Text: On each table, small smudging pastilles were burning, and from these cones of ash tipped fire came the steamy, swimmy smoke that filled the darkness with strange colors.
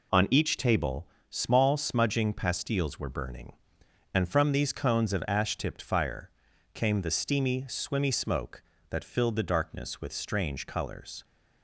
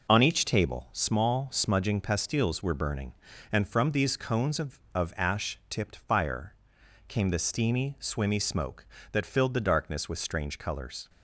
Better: first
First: pauses between "fire" and "came"; at 6.2 s; 0.44 s long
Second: says "of" twice; at 4.9 s // pauses between "fire" and "came"; noticeable; at 6.5 s; 0.54 s long

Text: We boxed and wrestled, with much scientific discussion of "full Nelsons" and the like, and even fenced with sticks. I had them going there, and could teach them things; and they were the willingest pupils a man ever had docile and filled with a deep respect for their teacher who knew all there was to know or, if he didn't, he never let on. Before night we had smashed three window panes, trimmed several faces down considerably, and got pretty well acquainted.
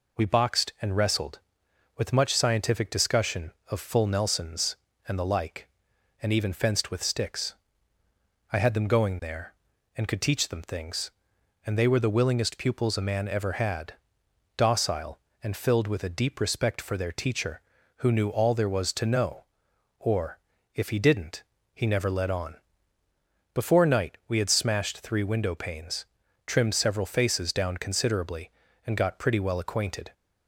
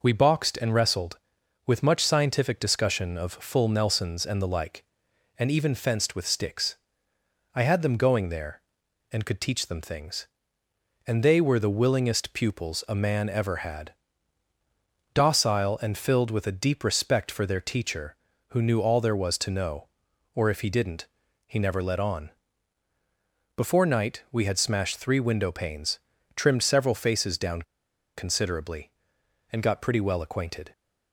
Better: first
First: pauses between "had" and "docile"; noticeable; at 13.9 s; 0.60 s long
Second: pauses between "had" and "docile"; at 13.9 s; 1.2 s long // pauses between "down" and "considerably"; noticeable; at 27.6 s; 0.53 s long

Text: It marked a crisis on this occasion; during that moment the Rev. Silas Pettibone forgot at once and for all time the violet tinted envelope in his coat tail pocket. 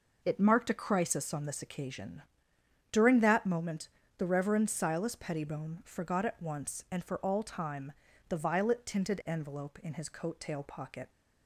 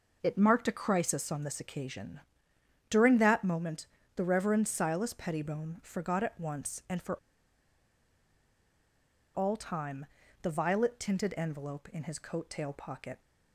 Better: first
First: pauses between "moment" and "the"; slight; at 3.8 s; 0.30 s long // pauses between "time" and "the"; slight; at 7.9 s; 0.36 s long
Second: pauses between "moment" and "the"; slight; at 3.8 s; 0.30 s long // pauses between "for" and "all"; strong; at 7.1 s; 2.1 s long // pauses between "time" and "the"; slight; at 10.0 s; 0.36 s long

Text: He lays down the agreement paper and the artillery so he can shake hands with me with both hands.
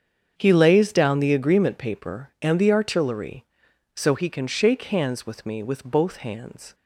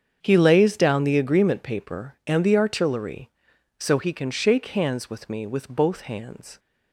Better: neither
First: starts louder than the rest; strong; until 1.3 s; 7.5 dB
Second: starts louder than the rest; strong; until 1.2 s; 7.5 dB

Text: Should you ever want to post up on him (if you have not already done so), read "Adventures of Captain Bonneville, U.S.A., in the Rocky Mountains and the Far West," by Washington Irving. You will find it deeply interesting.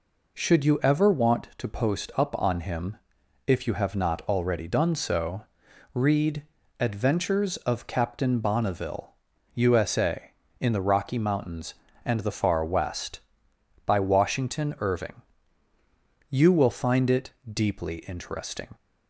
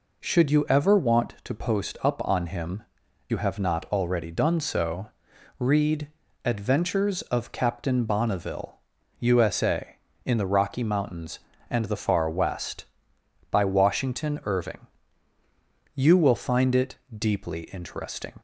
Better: first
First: pauses between "read" and "Adventures"; slight; at 6.4 s; 0.36 s long // pauses between "it" and "deeply"; slight; at 17.2 s; 0.24 s long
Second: skips "if"; at 3.0 s // pauses between "read" and "Adventures"; slight; at 6.0 s; 0.36 s long // pauses between "it" and "deeply"; slight; at 16.9 s; 0.24 s long

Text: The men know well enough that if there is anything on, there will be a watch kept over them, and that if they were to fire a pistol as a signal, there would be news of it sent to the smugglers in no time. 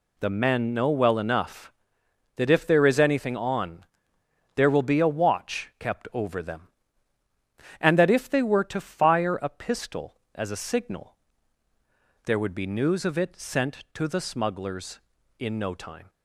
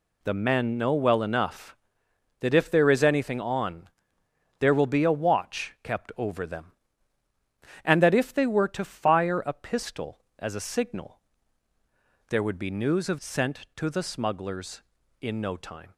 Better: first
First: none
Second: skips "it"; at 13.1 s

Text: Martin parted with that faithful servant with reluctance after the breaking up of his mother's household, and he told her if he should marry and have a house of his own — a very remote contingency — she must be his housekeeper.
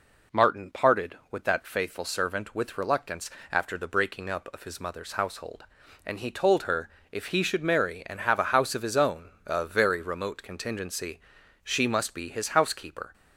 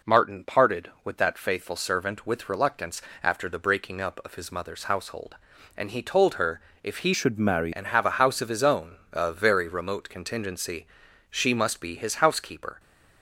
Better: first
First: pauses between "reluctance" and "after"; slight; at 3.2 s; 0.22 s long // pauses between "her" and "if"; slight; at 6.8 s; 0.22 s long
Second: pauses between "reluctance" and "after"; slight; at 3.0 s; 0.22 s long // pauses between "her" and "if"; slight; at 6.6 s; 0.22 s long // changes voice from "should" to "marry"; from 7.1 to 7.7 s; 0.6 s long

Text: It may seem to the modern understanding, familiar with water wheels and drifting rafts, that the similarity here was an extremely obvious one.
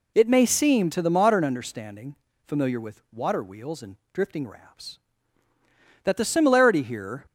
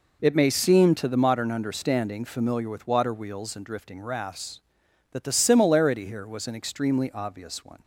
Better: second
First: pauses between "and" and "drifting"; slight; at 3.9 s; 0.16 s long // stops before "was an extremely obvious one"; at 7.2 s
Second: none

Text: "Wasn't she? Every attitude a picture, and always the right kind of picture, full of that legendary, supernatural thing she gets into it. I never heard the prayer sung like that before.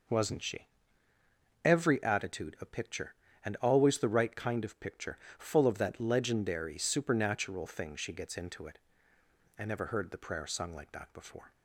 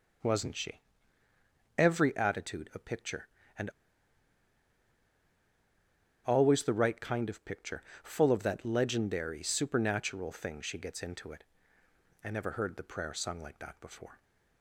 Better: first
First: none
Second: pauses between "and" and "always"; strong; at 3.7 s; 2.5 s long

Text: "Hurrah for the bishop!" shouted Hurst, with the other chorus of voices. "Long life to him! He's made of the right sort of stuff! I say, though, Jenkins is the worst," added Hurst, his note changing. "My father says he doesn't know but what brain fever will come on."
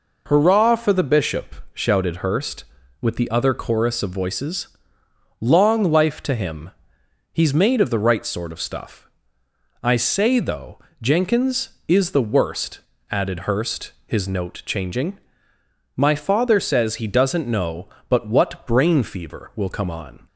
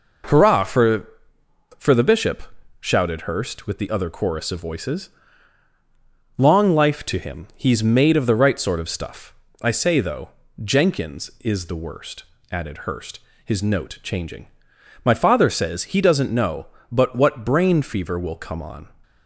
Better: first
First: none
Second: says "for" twice; at 1.7 s

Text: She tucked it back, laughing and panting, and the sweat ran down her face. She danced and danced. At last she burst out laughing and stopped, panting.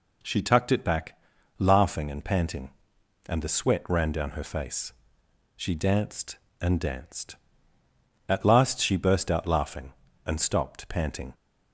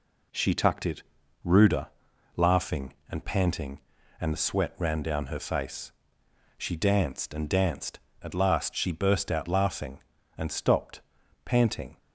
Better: first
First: none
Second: says "ruder" for "back"; at 1.4 s

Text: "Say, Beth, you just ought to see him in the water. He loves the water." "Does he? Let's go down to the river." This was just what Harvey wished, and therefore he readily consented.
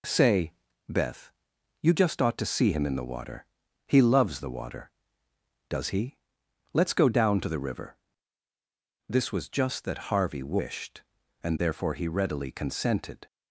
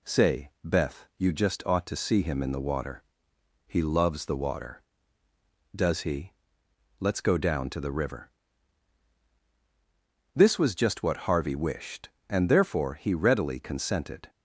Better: second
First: says "that" for "what"; at 9.8 s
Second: none

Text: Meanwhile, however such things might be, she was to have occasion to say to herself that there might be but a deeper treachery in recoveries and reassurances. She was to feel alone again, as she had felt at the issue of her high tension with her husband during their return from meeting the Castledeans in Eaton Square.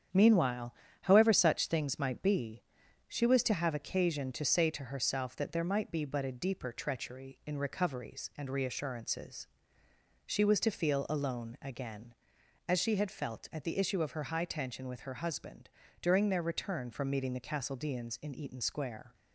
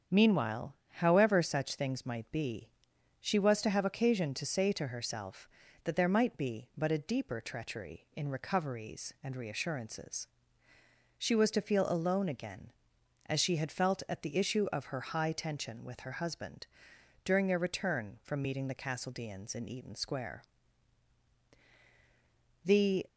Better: first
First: starts louder than the rest; strong; until 1.4 s; 8.5 dB // pauses between "husband" and "during"; slight; at 15.6 s; 0.32 s long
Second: starts louder than the rest; strong; until 1.2 s; 7 dB // pauses between "husband" and "during"; noticeable; at 16.6 s; 0.56 s long // goes on to say "The"; slight; from 22.6 s on; 0.44 s long

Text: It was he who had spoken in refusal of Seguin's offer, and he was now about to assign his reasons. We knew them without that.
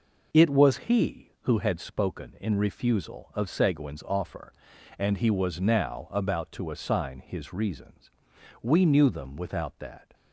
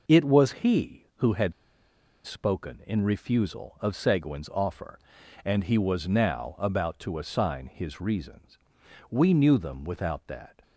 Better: first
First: none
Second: pauses between "had" and "spoken"; noticeable; at 1.5 s; 0.72 s long

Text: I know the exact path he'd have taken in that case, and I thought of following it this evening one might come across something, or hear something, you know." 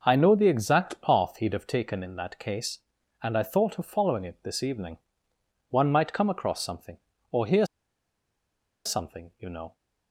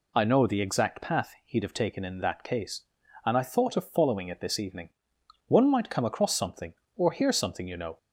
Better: second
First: pauses between "evening" and "one"; noticeable; at 4.9 s; 0.72 s long // pauses between "hear" and "something"; at 7.6 s; 1.2 s long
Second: pauses between "evening" and "one"; noticeable; at 4.8 s; 0.58 s long

